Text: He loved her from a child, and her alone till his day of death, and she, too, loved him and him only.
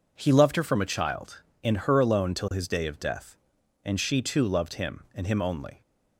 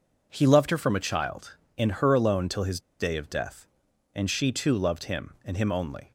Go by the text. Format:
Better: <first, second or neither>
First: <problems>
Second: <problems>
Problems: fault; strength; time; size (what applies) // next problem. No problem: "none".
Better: first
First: none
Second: pauses between "his" and "day"; slight; at 2.7 s; 0.20 s long